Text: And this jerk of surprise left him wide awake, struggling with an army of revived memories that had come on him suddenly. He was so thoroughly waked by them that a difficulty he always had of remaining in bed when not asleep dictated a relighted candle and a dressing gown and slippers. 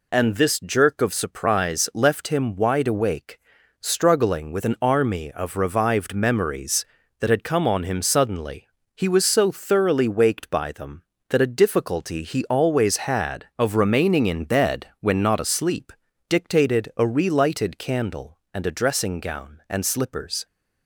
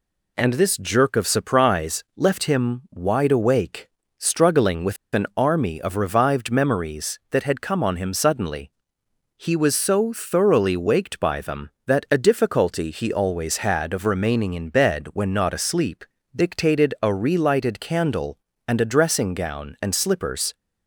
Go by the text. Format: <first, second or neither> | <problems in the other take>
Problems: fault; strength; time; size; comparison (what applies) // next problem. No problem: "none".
first | pauses between "with" and "an"; slight; at 4.9 s; 0.18 s long // pauses between "asleep" and "dictated"; slight; at 16.0 s; 0.30 s long; slight in the first